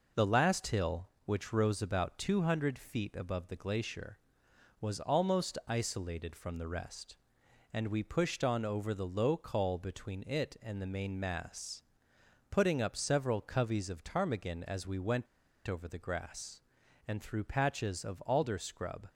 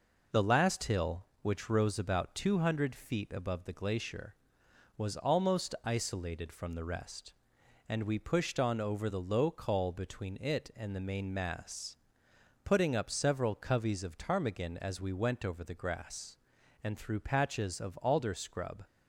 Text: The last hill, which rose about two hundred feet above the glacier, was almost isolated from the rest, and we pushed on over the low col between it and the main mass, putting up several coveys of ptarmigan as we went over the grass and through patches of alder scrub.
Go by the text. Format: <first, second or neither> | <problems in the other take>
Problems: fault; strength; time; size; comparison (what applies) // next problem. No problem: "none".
second | pauses between "went" and "over"; at 15.2 s; 0.40 s long